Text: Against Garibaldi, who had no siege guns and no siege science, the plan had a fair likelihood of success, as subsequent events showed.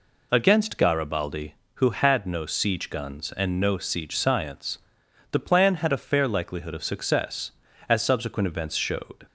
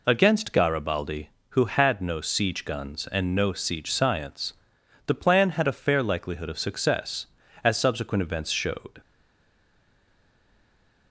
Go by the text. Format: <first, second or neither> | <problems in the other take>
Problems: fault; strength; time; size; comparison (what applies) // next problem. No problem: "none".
first | stays silent after the last word; noticeable; from 9.0 s on; 2.1 s long